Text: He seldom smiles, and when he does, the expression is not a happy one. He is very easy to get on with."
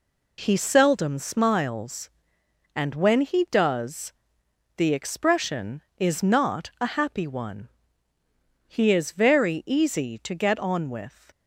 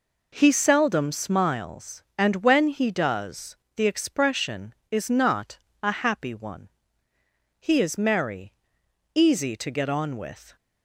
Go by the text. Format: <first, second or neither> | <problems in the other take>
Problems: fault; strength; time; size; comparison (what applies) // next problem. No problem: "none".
first | pauses between "not" and "a"; slight; at 5.5 s; 0.24 s long // says "merry" for "very"; at 7.9 s